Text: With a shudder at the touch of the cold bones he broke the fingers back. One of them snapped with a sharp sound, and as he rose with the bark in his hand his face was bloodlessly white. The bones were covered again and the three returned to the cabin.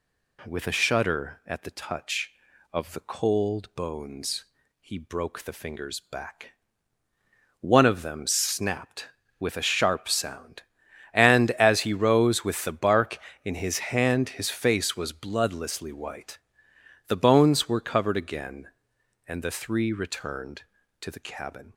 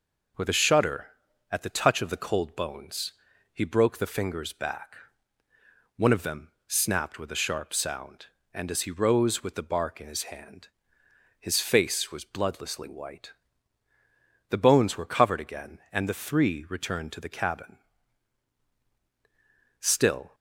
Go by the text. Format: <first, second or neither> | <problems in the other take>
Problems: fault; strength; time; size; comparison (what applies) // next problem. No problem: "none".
first | pauses between "bones" and "he"; at 3.1 s; 0.40 s long; slight in the first // pauses between "them" and "snapped"; slight; at 6.4 s; 0.18 s long // pauses between "hand" and "his"; noticeable; at 10.6 s; 0.72 s long // goes on to say "Still"; from 19.7 s on; 0.56 s long